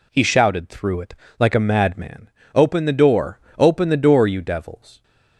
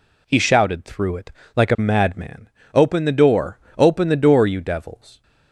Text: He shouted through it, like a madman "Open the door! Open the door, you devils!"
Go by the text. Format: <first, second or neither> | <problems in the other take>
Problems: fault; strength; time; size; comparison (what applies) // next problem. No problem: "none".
neither | pauses between "madman" and "Open"; slight; the same in both